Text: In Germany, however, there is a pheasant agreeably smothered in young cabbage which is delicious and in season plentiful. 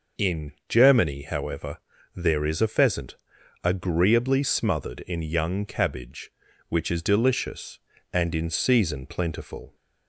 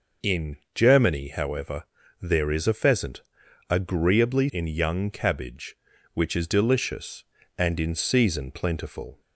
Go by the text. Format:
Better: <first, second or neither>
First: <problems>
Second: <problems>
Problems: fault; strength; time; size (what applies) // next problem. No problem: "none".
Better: first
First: pauses between "In" and "Germany"; slight; at 0.5 s; 0.16 s long // pauses between "pheasant" and "agreeably"; noticeable; at 3.1 s; 0.48 s long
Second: pauses between "In" and "Germany"; slight; at 0.5 s; 0.18 s long // pauses between "pheasant" and "agreeably"; noticeable; at 3.2 s; 0.48 s long // skips "smothered"; at 4.4 s